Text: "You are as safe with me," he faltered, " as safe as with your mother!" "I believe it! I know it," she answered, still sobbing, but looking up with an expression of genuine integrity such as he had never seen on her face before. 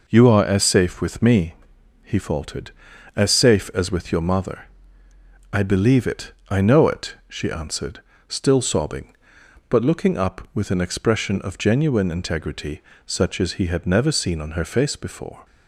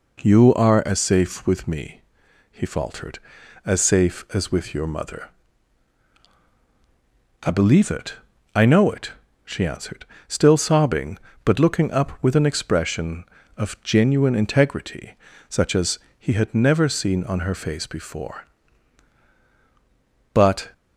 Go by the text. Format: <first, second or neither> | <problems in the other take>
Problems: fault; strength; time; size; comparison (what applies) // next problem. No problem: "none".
first | pauses between "integrity" and "such"; slight; at 15.1 s; 0.34 s long; slight in the first // pauses between "as" and "he"; slight; at 15.9 s; 0.20 s long // goes on to say "But"; slight; from 20.3 s on; 0.40 s long